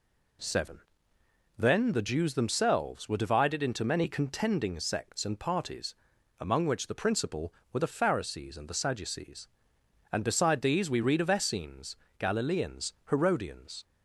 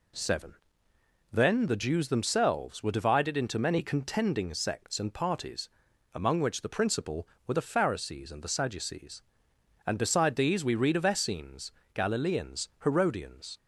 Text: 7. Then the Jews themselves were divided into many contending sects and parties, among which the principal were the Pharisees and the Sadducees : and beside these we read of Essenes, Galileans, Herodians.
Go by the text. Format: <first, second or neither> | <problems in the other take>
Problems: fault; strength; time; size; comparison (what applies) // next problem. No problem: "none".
neither | none